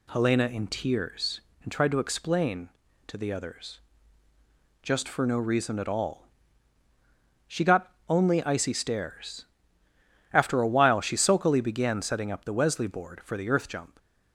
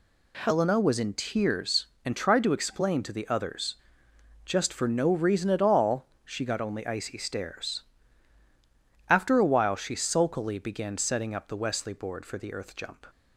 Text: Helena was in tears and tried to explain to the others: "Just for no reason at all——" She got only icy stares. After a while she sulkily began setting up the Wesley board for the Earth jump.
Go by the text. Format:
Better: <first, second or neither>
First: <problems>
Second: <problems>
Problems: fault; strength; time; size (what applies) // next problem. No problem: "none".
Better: second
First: skips "was"; at 0.4 s // pauses between "got" and "only"; slight; at 7.9 s; 0.16 s long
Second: none